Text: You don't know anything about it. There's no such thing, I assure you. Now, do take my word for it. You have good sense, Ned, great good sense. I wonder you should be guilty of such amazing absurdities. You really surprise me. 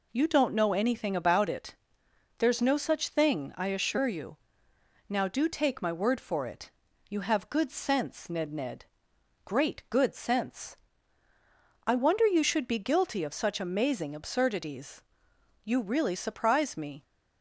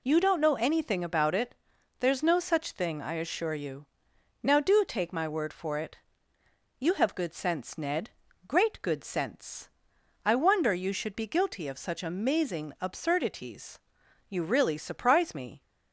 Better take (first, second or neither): second